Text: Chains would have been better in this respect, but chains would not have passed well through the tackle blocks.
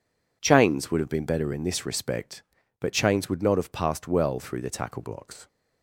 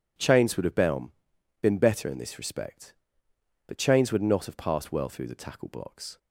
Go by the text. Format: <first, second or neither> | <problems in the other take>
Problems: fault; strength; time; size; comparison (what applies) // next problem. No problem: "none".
first | says "been" twice; at 1.6 s